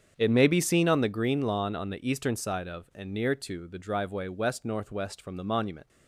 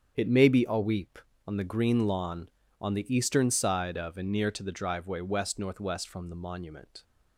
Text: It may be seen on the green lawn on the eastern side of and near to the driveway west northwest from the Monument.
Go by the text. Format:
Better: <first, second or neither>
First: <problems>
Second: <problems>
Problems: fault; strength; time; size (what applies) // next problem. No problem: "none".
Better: first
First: starts louder than the rest; strong; until 1.1 s; 7.5 dB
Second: starts louder than the rest; strong; until 1.1 s; 8 dB // says "aweep" for "seen"; at 0.6 s